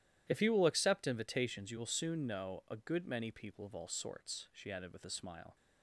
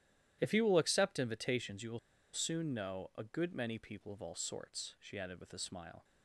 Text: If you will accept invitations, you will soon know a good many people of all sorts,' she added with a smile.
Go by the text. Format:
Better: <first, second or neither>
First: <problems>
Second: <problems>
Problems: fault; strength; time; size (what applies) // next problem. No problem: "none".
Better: first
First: starts louder than the rest; strong; until 1.2 s; 12.5 dB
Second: starts louder than the rest; strong; until 1.4 s; 12.5 dB // pauses between "will" and "soon"; slight; at 1.9 s; 0.34 s long